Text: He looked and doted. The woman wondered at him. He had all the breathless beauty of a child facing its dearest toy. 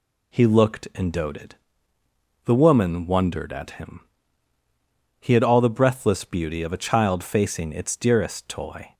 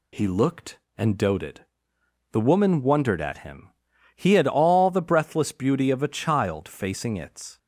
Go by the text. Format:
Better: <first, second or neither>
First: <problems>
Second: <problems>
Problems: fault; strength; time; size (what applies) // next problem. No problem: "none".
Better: first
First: none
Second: stops before "dearest toy"; at 7.5 s